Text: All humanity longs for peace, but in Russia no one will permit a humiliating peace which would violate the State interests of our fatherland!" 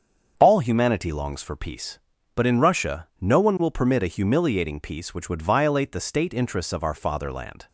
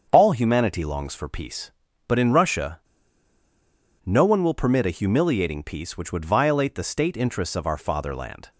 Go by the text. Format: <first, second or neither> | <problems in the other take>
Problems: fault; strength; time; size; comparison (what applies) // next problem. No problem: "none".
first | starts louder than the rest; until 1.1 s; 7 dB; also in the first // pauses between "Russia" and "no"; strong; at 2.7 s; 1.2 s long